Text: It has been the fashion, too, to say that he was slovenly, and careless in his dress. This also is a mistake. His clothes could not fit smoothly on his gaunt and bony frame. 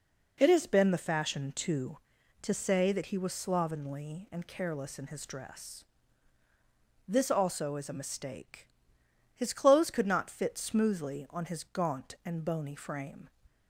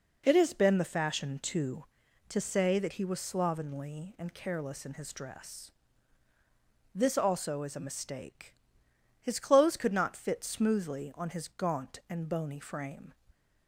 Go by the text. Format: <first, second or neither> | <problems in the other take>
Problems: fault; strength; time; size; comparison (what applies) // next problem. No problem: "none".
neither | none